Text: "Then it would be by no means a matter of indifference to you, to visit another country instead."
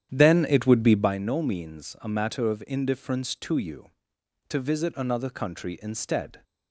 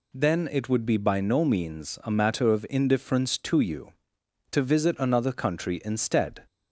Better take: second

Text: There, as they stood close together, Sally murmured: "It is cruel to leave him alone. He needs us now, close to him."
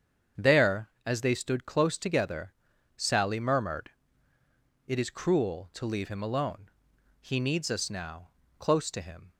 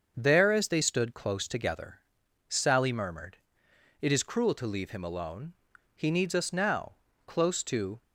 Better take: first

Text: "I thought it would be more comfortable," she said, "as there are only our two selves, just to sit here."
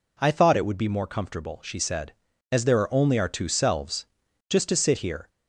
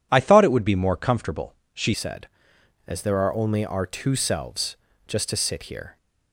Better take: first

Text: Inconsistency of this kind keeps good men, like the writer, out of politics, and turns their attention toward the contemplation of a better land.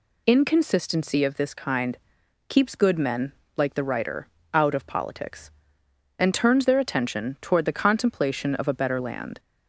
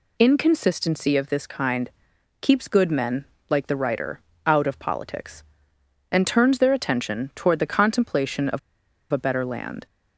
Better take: first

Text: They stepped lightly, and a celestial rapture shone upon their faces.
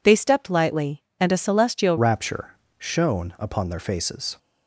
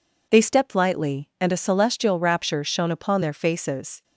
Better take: second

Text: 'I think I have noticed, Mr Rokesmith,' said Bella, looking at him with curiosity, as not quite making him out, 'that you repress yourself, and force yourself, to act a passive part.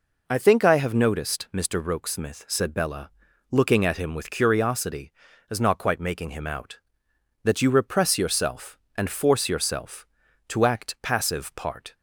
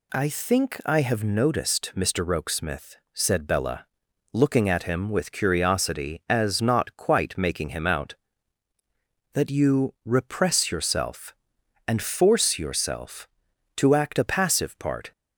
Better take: second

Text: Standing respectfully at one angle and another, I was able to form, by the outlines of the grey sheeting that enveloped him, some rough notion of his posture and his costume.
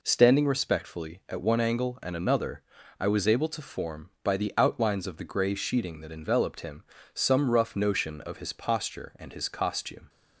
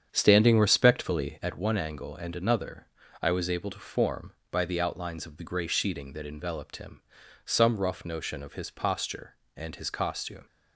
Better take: first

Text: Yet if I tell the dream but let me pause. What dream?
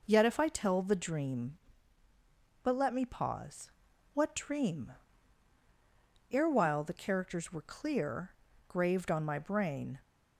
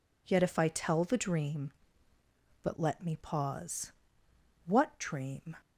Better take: second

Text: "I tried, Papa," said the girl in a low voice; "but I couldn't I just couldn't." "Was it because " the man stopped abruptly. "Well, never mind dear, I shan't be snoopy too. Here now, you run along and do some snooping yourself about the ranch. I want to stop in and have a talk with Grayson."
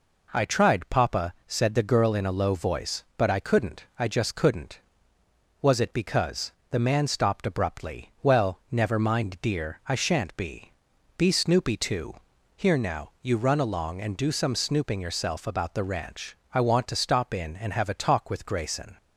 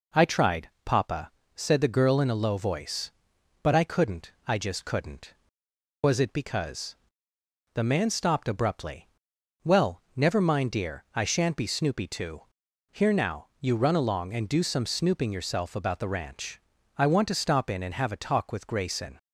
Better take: second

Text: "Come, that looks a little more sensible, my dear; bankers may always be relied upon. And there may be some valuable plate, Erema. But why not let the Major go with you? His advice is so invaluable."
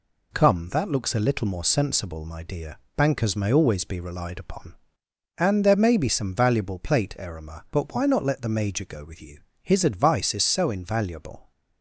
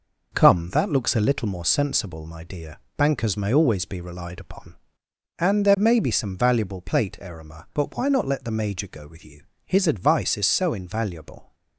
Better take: first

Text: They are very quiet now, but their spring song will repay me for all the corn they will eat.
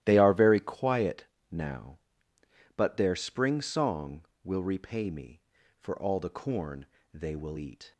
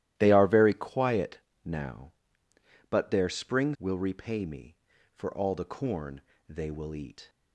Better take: first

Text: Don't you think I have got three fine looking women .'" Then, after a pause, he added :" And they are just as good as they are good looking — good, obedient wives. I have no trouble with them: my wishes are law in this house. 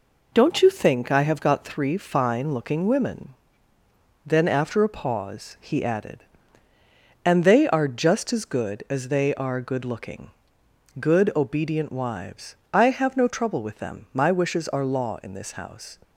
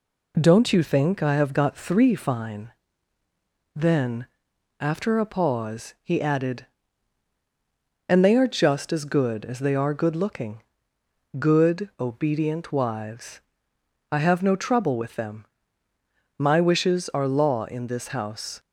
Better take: first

